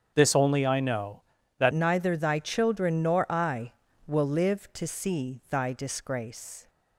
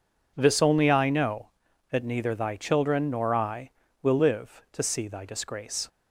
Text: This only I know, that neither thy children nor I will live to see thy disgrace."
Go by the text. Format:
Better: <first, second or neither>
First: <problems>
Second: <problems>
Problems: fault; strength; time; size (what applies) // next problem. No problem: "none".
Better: second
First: starts louder than the rest; strong; until 1.1 s; 7.5 dB // changes voice at "neither"; from 1.7 s on; 4.9 s long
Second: none